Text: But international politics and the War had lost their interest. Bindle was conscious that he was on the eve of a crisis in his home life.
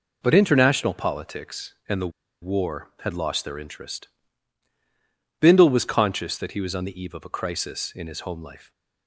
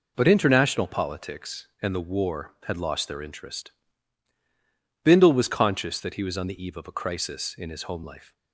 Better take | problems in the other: second | pauses between "the" and "War"; slight; at 2.1 s; 0.31 s long

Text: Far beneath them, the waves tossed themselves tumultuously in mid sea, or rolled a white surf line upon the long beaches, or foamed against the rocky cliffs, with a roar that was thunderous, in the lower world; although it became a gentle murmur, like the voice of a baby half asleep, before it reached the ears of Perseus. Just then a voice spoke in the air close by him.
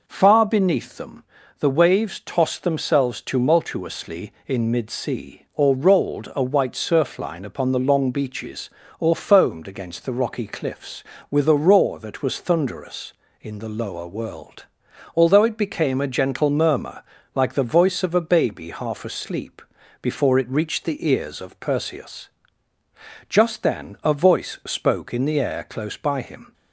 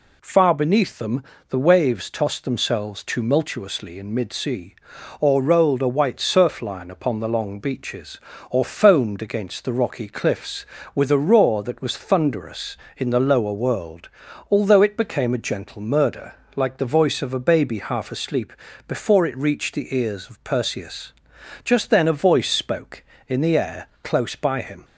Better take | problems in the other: first | says "murder" for "murmur"; at 15.8 s // pauses between "air" and "close"; slight; at 23.8 s; 0.16 s long

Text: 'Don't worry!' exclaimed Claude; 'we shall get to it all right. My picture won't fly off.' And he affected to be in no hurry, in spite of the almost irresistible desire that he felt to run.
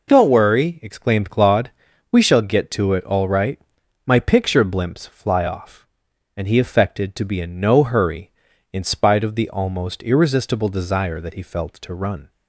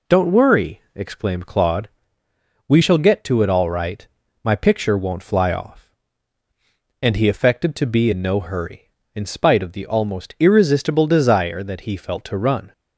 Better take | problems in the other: second | says "blimps" for "won't"; at 4.6 s

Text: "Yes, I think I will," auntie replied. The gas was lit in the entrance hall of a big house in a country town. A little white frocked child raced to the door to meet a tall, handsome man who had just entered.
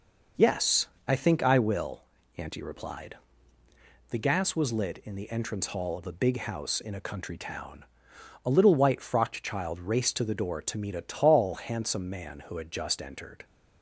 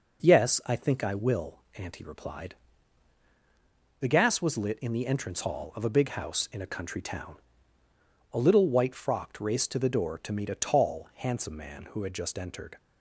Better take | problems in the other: first | skips "child"; at 9.4 s

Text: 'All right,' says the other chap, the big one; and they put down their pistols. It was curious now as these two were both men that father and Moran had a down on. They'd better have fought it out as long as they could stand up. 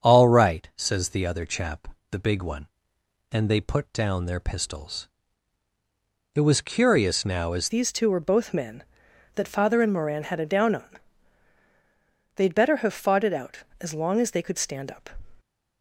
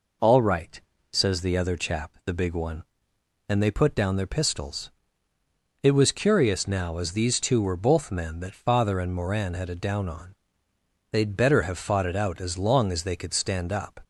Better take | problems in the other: second | starts louder than the rest; strong; until 1.1 s; 7 dB // changes voice at "these"; from 7.6 s on; 7.5 s long

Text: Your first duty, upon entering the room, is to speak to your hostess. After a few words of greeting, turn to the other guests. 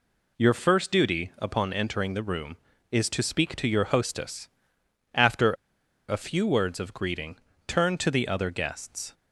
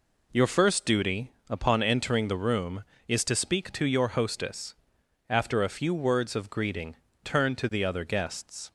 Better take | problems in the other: second | pauses between "After" and "a"; noticeable; at 5.5 s; 0.55 s long

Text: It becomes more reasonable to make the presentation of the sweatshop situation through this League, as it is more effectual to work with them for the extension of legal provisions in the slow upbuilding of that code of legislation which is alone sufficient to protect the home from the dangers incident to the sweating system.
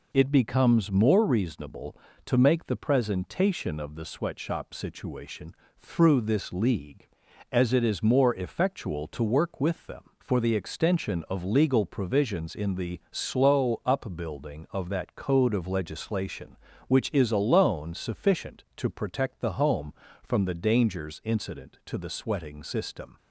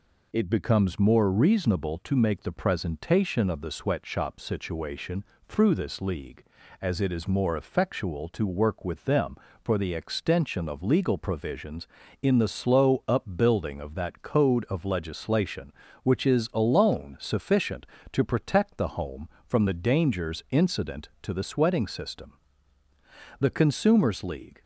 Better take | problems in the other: first | pauses between "situation" and "through"; slight; at 5.2 s; 0.24 s long; slight in the first // goes on to say "The Consumers League"; noticeable; from 23.4 s on; 1.2 s long

